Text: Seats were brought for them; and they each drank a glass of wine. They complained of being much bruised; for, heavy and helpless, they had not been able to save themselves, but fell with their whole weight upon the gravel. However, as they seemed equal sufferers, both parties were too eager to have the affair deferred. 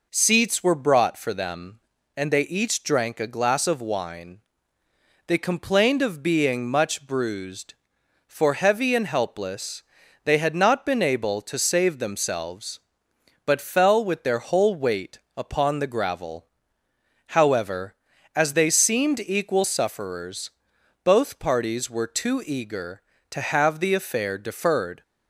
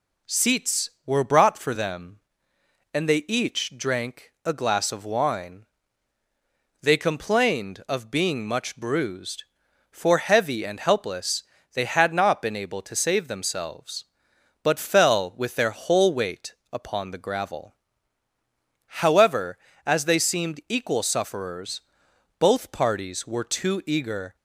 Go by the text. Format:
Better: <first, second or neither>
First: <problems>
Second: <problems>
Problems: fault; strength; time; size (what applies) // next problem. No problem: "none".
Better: first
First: pauses between "weight" and "upon"; slight; at 15.1 s; 0.18 s long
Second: pauses between "weight" and "upon"; slight; at 16.5 s; 0.18 s long // stops before "to have the affair deferred"; at 24.3 s